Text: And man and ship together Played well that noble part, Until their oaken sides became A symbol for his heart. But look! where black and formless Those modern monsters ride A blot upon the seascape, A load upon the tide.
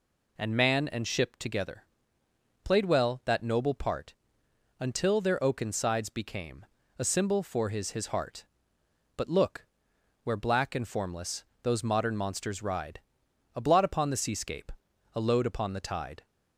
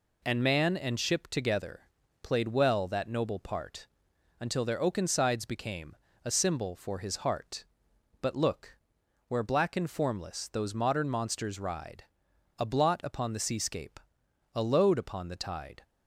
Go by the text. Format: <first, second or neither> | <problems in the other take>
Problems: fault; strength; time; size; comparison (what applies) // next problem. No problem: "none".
second | pauses between "together" and "Played"; noticeable; at 1.8 s; 0.80 s long; also in the second // pauses between "became" and "A"; slight; at 6.6 s; 0.32 s long; slight in the second // says "his" twice; at 7.9 s // pauses between "formless" and "Those"; slight; at 11.4 s; 0.18 s long // pauses between "ride" and "A"; noticeable; at 12.9 s; 0.54 s long; noticeable in the second